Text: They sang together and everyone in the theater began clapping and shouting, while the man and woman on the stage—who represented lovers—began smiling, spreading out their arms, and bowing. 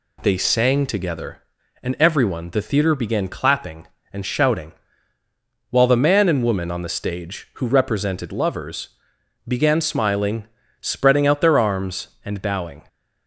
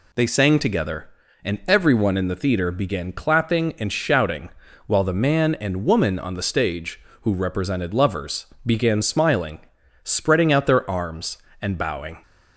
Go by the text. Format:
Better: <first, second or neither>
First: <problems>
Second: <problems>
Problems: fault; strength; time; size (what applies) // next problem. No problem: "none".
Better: second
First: skips "in"; at 2.4 s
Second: none